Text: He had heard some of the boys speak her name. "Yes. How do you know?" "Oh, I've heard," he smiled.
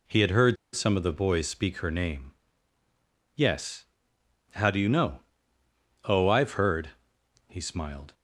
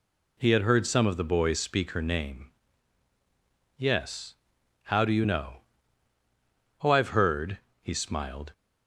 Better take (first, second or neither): second